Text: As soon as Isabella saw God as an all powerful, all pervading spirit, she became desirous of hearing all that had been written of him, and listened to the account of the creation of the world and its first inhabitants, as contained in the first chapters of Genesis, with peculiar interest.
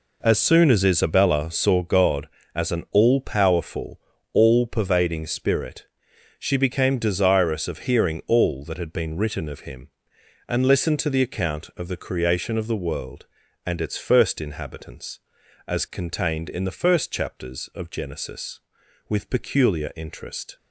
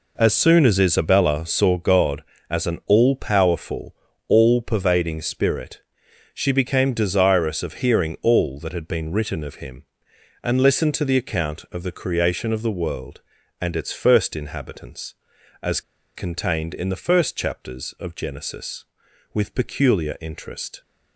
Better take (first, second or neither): first